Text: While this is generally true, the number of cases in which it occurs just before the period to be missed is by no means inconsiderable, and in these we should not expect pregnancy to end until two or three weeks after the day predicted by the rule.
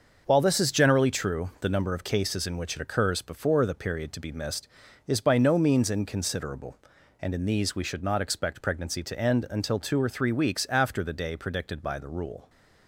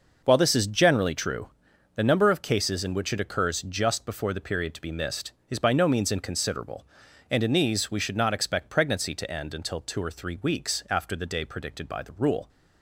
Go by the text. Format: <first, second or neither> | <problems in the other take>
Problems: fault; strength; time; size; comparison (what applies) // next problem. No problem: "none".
second | starts louder than the rest; until 1.2 s; 6.5 dB // skips "just"; at 3.2 s